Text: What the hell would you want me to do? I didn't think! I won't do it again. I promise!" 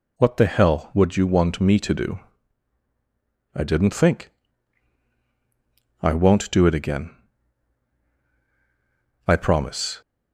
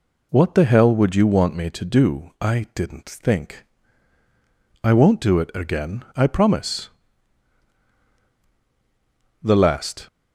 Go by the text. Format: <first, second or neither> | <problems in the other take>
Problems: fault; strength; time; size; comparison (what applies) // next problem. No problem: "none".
first | goes on to say "The last"; noticeable; from 9.4 s on; 0.64 s long